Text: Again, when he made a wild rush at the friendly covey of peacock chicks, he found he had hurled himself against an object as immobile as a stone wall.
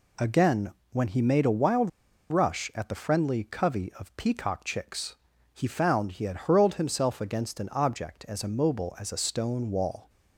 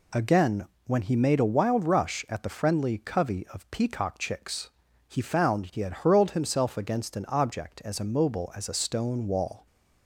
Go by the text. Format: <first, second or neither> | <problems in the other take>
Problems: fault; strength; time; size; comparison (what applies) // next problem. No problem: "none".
second | pauses between "wild" and "rush"; at 1.8 s; 0.40 s long